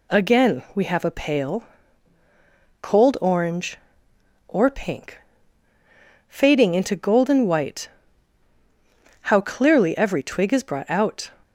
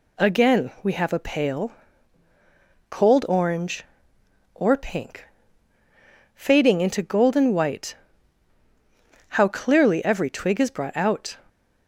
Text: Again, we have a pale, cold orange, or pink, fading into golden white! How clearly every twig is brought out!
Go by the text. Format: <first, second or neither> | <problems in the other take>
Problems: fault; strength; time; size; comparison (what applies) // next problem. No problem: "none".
neither | none